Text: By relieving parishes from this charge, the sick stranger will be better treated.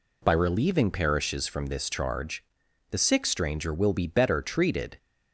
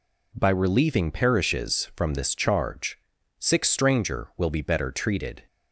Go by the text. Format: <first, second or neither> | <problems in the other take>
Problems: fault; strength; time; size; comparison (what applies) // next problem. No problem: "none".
first | skips "the"; at 3.1 s